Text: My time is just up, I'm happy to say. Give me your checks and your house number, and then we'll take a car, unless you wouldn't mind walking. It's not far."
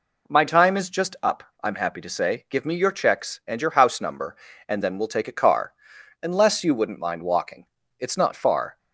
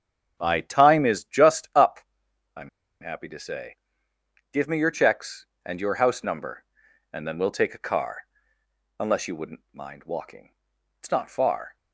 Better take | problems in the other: first | starts louder than the rest; strong; until 1.4 s; 8.5 dB // pauses between "I'm" and "happy"; slight; at 2.6 s; 0.31 s long

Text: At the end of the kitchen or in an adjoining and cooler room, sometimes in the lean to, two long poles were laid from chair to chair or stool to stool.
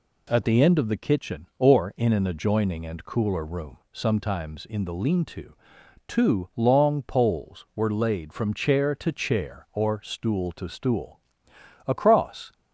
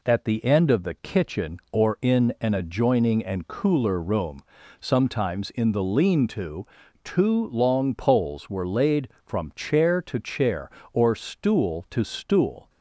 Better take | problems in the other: second | goes on to say "Across"; noticeable; from 11.8 s on; 0.66 s long

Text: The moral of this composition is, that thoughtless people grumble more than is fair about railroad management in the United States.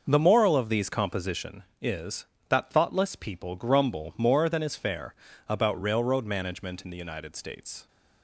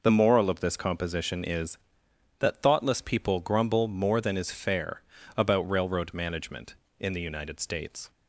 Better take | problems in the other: second | says "these" for "this"; at 0.6 s // pauses between "fair" and "about"; slight; at 5.1 s; 0.34 s long; slight in the second

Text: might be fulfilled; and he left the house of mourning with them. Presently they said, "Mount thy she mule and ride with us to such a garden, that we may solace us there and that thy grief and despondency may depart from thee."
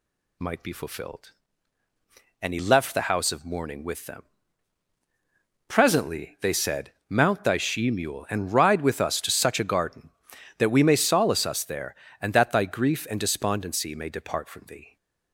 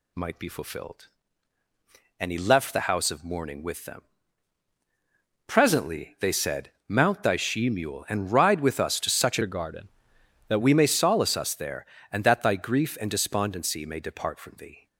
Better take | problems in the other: first | changes voice from "a" to "that"; from 9.4 to 10.6 s; 1.2 s long

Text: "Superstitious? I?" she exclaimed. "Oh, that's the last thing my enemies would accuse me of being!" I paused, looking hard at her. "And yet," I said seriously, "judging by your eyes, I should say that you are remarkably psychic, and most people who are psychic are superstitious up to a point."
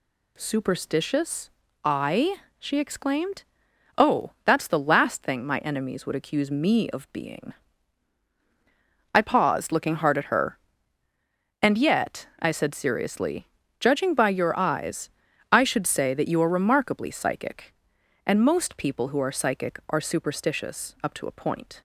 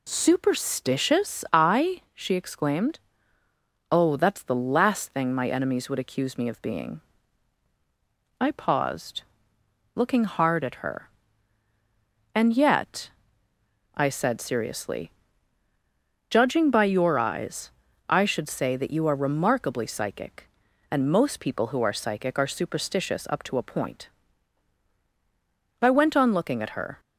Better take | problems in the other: first | goes on to say "I went on looking at her"; noticeable; from 25.8 s on; 1.1 s long

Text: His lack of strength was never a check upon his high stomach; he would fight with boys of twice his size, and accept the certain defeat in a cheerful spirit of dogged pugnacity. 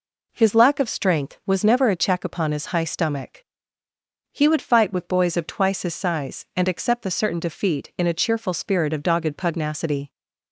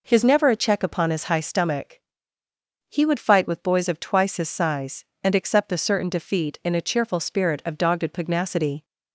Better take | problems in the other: first | skips "lack of strength was"; at 0.2 s

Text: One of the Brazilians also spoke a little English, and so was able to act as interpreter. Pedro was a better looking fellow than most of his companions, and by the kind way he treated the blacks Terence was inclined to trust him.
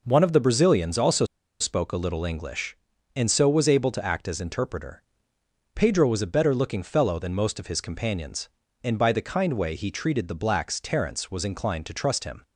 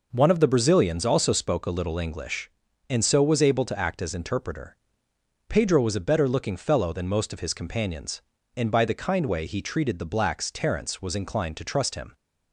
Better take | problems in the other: second | pauses between "also" and "spoke"; at 1.2 s; 0.36 s long

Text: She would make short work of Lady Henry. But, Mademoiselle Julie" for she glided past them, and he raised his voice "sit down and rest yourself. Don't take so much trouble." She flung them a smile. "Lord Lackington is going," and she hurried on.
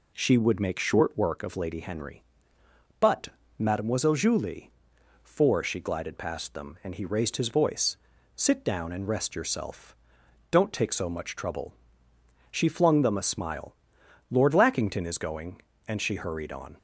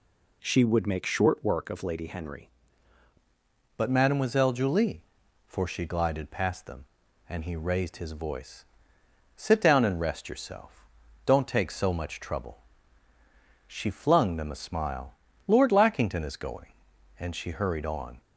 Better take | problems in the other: first | changes voice at "But"; from 3.7 s on; 14.4 s long // pauses between "voice" and "sit"; noticeable; at 8.6 s; 0.72 s long; also in the first

